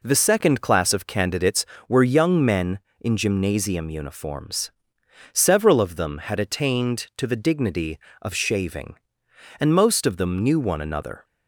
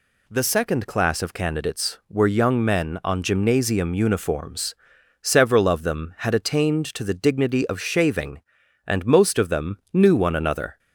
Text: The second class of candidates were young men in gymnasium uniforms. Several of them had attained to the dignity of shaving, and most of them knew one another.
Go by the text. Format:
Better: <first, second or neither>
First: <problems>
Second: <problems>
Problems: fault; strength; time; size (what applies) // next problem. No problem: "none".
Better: first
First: none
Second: says "on" for "in"; at 3.0 s